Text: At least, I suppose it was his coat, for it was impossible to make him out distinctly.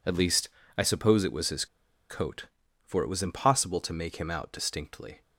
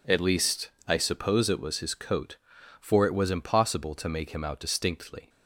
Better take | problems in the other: second | pauses between "his" and "coat"; at 1.6 s; 0.44 s long

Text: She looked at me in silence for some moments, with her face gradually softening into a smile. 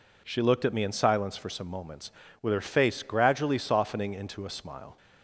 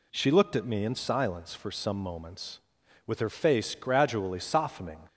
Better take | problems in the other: first | stops before "into a smile"; at 5.0 s

